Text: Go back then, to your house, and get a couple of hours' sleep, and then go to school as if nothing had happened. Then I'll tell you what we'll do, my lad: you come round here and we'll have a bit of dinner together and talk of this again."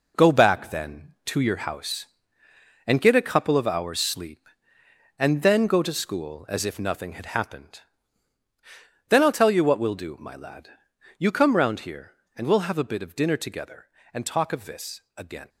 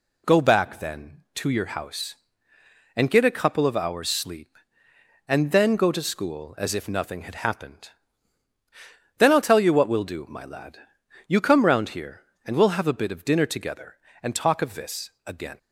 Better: second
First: gets quieter; throughout; 6.5 dB // pauses between "this" and "again"; slight; at 15.0 s; 0.16 s long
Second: pauses between "this" and "again"; slight; at 15.0 s; 0.16 s long

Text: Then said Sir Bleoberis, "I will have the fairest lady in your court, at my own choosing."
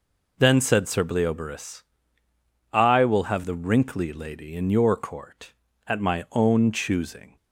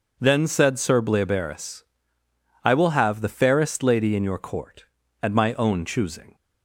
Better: second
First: says "wrinkly" for "fairest"; at 3.5 s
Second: none

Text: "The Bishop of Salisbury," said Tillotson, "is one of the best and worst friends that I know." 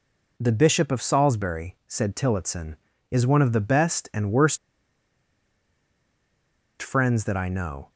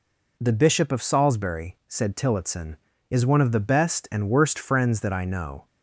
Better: second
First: pauses between "worst" and "friends"; strong; at 4.5 s; 2.2 s long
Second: none

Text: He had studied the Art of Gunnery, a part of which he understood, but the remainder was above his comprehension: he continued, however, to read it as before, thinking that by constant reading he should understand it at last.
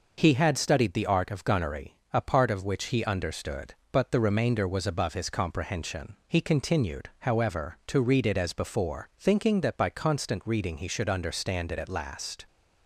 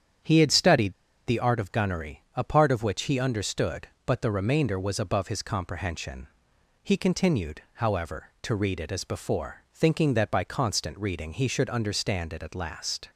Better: first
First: none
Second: starts louder than the rest; strong; until 1.5 s; 8.5 dB // pauses between "studied" and "the"; slight; at 0.9 s; 0.34 s long

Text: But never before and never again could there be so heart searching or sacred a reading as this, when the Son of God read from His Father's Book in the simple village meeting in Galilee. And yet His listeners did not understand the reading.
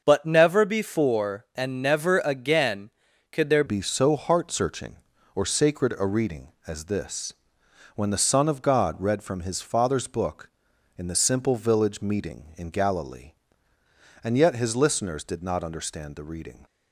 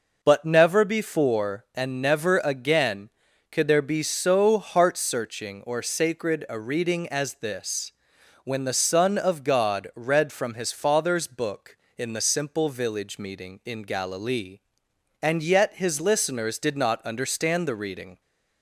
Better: second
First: starts louder than the rest; noticeable; until 1.0 s; 6 dB // changes voice at "be"; from 3.6 s on; 13.0 s long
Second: none

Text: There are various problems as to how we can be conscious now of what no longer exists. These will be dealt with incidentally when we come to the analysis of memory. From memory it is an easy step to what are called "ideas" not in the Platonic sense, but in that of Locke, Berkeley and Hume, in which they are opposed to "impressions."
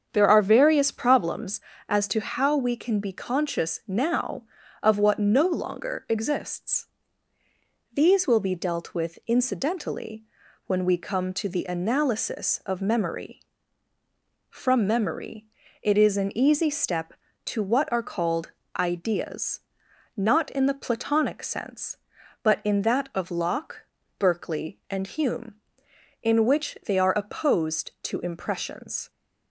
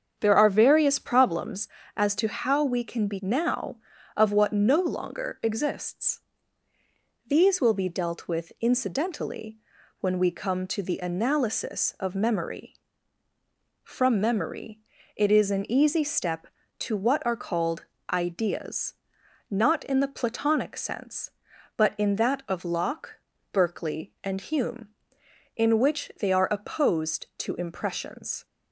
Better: first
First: starts louder than the rest; strong; until 1.1 s; 7.5 dB // pauses between "incidentally" and "when"; at 10.2 s; 0.42 s long // pauses between "memory" and "it"; slight; at 15.4 s; 0.36 s long // pauses between "called" and "ideas"; slight; at 18.5 s; 0.28 s long // pauses between "ideas" and "not"; noticeable; at 19.5 s; 0.56 s long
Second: starts louder than the rest; strong; until 1.2 s; 7.5 dB // skips "conscious"; at 3.1 s // pauses between "incidentally" and "when"; at 9.5 s; 0.42 s long // pauses between "memory" and "it"; slight; at 14.7 s; 0.36 s long // pauses between "called" and "ideas"; slight; at 17.8 s; 0.28 s long // pauses between "ideas" and "not"; noticeable; at 18.9 s; 0.56 s long

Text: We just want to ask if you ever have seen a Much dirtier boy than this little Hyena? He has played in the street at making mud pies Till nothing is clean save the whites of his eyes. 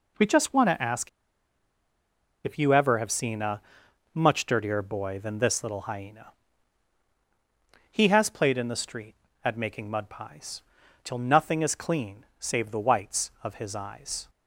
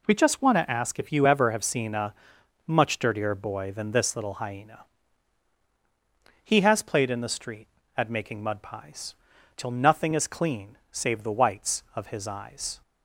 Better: second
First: pauses between "ask" and "if"; strong; at 1.0 s; 1.3 s long // pauses between "a" and "Much"; noticeable; at 3.6 s; 0.52 s long // pauses between "pies" and "Till"; at 10.6 s; 0.42 s long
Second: pauses between "a" and "Much"; noticeable; at 2.1 s; 0.52 s long // pauses between "pies" and "Till"; at 9.1 s; 0.42 s long

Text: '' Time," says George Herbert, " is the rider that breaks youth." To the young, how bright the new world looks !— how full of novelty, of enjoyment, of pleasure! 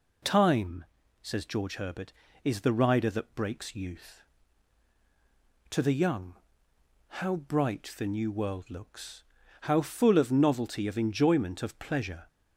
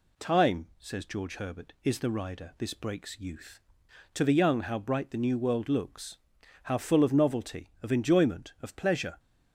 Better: first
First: none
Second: says "this" for "that"; at 2.5 s

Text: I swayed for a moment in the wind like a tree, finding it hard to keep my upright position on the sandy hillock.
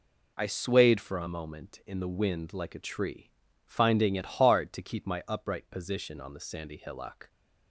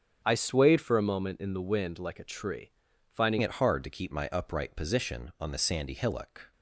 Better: first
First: none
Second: starts louder than the rest; until 1.2 s; 6.5 dB // changes voice at "it"; from 3.3 s on; 3.2 s long

